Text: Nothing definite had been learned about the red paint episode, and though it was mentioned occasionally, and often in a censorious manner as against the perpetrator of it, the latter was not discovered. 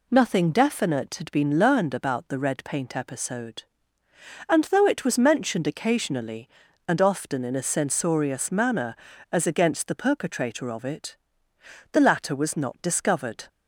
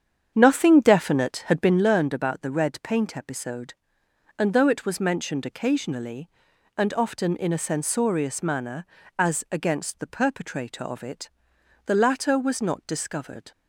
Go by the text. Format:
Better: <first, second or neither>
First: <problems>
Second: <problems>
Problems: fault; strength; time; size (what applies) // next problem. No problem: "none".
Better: first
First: none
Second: starts louder than the rest; strong; until 1.9 s; 8 dB